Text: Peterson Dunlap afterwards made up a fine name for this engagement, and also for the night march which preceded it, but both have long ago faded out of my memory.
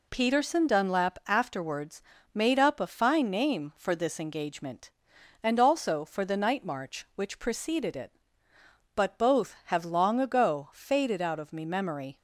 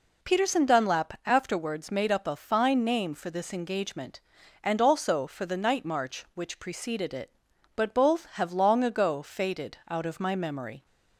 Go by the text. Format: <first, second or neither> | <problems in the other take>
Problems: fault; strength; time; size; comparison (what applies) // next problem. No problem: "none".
second | pauses between "afterwards" and "made"; slight; at 2.0 s; 0.32 s long // says "me" for "my"; at 11.5 s